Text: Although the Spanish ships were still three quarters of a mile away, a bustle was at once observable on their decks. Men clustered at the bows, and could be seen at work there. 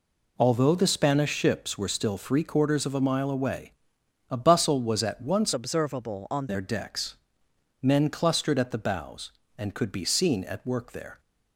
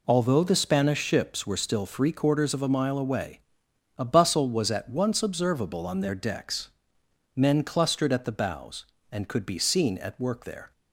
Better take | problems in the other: second | changes voice from "observable" to "on"; from 5.5 to 6.4 s; 0.9 s long

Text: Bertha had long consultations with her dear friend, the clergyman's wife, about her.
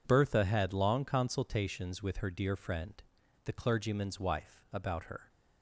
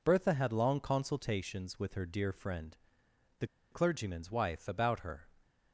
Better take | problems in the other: first | pauses between "the" and "clergyman's"; slight; at 3.4 s; 0.26 s long

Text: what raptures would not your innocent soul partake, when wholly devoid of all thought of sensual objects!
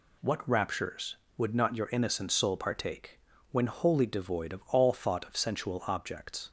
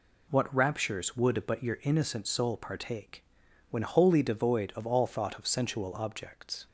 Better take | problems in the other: first | says "but" for "not"; at 1.4 s

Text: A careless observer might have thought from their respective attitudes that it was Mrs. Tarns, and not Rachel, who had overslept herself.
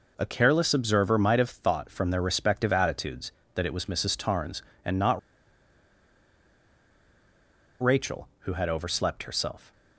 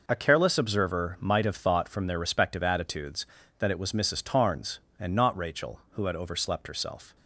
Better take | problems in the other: second | pauses between "not" and "Rachel"; strong; at 5.1 s; 2.6 s long

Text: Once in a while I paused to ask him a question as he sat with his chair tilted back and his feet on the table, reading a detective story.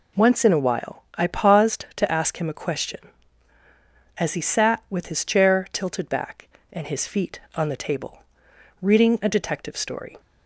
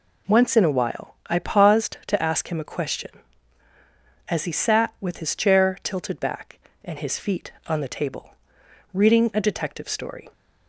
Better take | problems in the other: neither | none

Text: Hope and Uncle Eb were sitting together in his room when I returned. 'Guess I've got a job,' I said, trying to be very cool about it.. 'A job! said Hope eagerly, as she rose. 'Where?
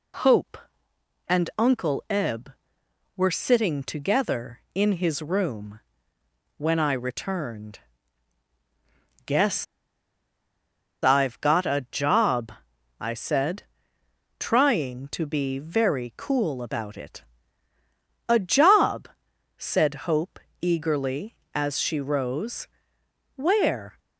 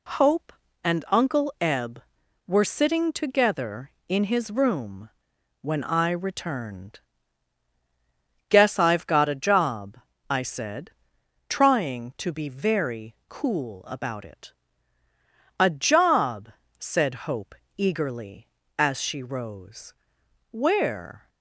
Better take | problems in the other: second | pauses between "room" and "when"; noticeable; at 5.8 s; 0.76 s long; noticeable in the second // pauses between "Guess" and "I've"; strong; at 9.6 s; 1.3 s long // pauses between "Hope" and "eagerly"; slight; at 20.3 s; 0.24 s long; slight in the second

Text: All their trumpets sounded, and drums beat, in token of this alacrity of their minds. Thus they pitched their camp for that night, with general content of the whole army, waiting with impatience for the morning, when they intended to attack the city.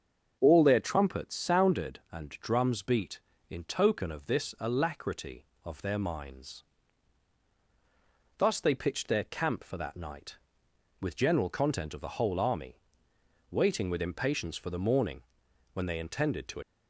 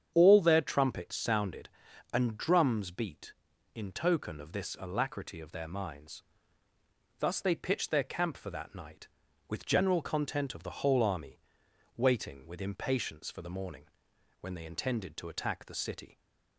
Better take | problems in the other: second | starts louder than the rest; until 1.4 s; 7 dB; strong in the second // stops before "attack the city"; at 16.6 s

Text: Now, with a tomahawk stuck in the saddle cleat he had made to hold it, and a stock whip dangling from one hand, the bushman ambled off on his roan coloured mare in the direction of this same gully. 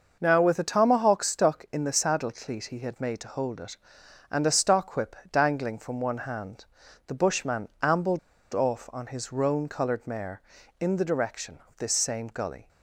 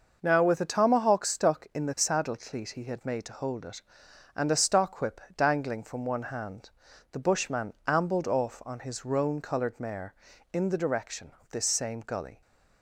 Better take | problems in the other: second | pauses between "whip" and "dangling"; slight; at 5.1 s; 0.16 s long; slight in the second // pauses between "ambled" and "off"; slight; at 8.1 s; 0.34 s long

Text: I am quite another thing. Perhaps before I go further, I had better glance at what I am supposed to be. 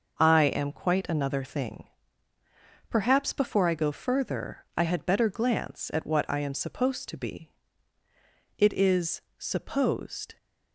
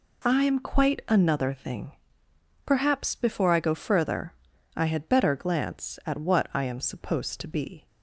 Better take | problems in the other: second | goes on to say "It is supposed"; strong; from 8.5 s on; 1.8 s long

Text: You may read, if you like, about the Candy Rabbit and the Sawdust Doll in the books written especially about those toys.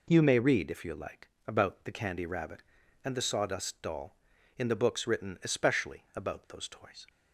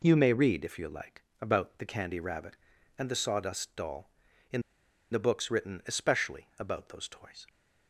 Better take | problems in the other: first | pauses between "in" and "the"; noticeable; at 4.6 s; 0.50 s long

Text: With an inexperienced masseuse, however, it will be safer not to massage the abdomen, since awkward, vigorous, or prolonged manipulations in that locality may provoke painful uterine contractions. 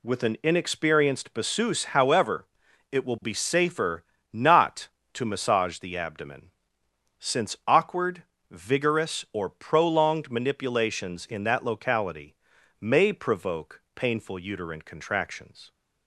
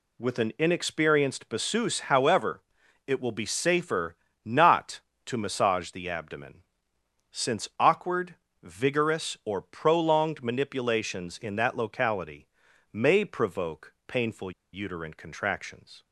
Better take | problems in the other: first | pauses between "safer" and "not"; slight; at 4.1 s; 0.30 s long; slight in the first // pauses between "locality" and "may"; at 12.4 s; 0.44 s long; also in the first // pauses between "painful" and "uterine"; slight; at 14.5 s; 0.21 s long

